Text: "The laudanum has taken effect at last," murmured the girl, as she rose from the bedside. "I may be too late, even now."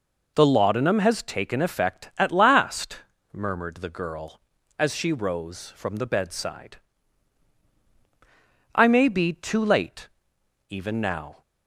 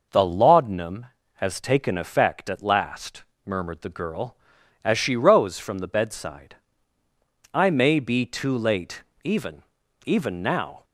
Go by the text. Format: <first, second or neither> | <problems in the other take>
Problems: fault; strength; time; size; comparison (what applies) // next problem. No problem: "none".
first | says "even" twice; at 10.0 s